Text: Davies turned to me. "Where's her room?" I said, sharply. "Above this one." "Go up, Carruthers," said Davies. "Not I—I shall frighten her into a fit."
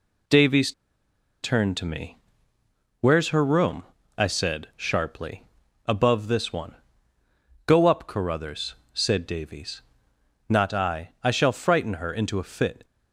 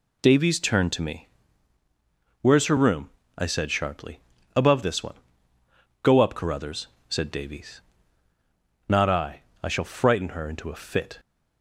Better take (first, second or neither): second